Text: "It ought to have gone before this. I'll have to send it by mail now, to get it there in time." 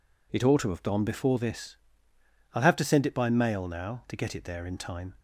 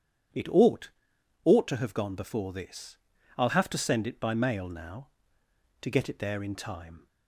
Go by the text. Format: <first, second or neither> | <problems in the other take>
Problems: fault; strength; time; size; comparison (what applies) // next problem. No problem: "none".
first | starts louder than the rest; strong; until 1.8 s; 9 dB // says "ought" twice; at 1.4 s